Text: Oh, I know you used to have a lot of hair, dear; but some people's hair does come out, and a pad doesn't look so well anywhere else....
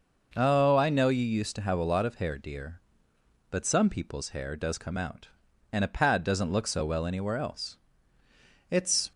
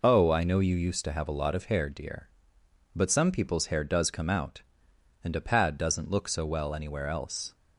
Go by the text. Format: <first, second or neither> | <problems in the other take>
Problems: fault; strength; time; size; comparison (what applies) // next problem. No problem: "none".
second | goes on to say "It's"; slight; from 8.7 s on; 0.40 s long